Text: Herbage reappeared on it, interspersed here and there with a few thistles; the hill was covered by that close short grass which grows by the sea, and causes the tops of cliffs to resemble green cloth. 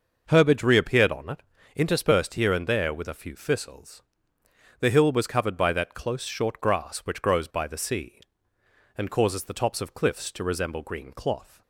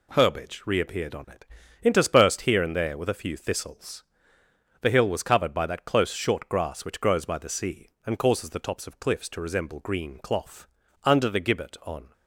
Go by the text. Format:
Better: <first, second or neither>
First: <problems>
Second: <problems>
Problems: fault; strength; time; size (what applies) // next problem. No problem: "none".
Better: first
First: none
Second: goes on to say "Under the gibbet on"; noticeable; from 11.0 s on; 1.0 s long